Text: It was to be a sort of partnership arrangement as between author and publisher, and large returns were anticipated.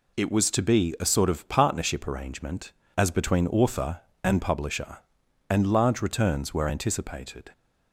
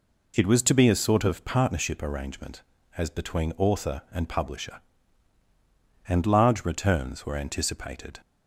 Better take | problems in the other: neither | none

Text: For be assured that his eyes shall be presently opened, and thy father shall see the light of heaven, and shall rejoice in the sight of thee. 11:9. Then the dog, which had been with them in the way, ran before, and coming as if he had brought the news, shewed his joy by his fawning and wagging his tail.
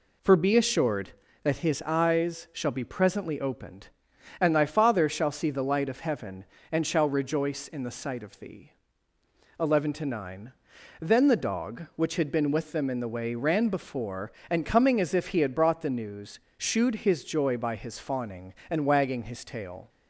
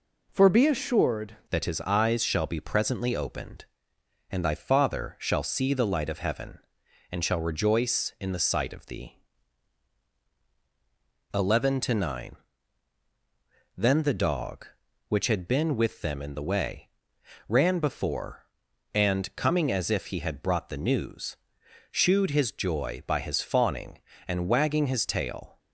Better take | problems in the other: first | changes voice at "that"; from 1.5 s on; 24.0 s long

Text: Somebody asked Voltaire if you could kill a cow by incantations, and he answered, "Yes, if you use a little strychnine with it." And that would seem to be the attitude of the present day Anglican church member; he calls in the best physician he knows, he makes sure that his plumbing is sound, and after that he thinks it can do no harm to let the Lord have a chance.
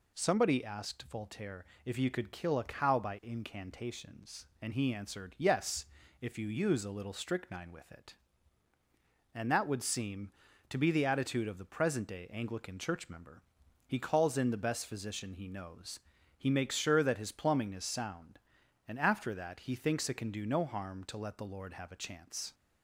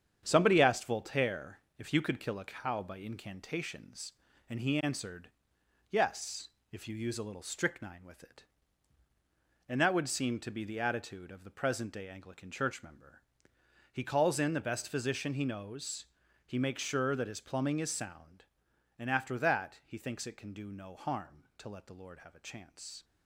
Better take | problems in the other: first | gets quieter; throughout; 7 dB // pauses between "Voltaire" and "if"; slight; at 1.5 s; 0.20 s long; slight in the first

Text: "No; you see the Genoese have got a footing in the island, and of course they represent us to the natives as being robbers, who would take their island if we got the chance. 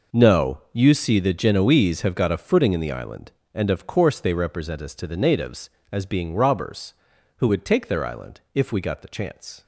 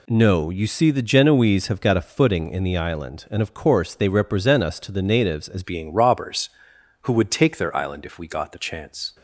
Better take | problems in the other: first | changes voice at "being"; from 5.6 s on; 3.5 s long

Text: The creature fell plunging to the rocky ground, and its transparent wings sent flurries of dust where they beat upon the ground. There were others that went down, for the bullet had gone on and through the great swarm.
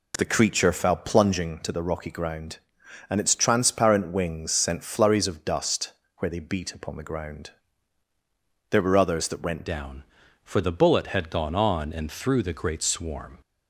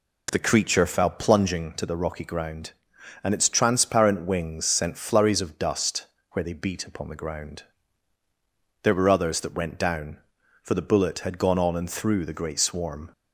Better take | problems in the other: second | pauses between "dust" and "where"; slight; at 5.9 s; 0.28 s long; slight in the second // changes voice at "down"; from 9.6 s on; 3.7 s long

